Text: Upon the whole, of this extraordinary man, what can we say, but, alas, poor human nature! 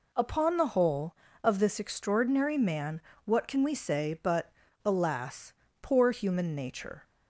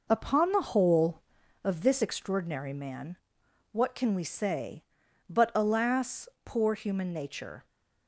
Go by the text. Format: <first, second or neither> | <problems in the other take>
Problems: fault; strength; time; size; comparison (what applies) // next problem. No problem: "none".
first | starts louder than the rest; noticeable; until 1.6 s; 5 dB